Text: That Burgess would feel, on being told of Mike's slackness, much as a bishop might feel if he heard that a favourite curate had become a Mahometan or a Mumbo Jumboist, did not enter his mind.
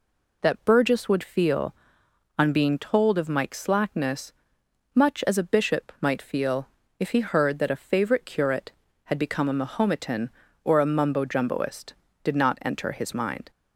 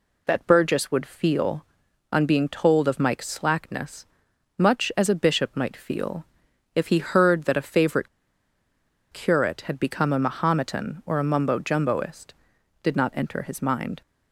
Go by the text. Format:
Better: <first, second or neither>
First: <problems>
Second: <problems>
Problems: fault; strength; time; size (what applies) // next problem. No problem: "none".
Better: first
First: pauses between "feel" and "if"; slight; at 6.6 s; 0.32 s long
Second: pauses between "feel" and "if"; noticeable; at 6.2 s; 0.50 s long // pauses between "favourite" and "curate"; at 8.0 s; 1.0 s long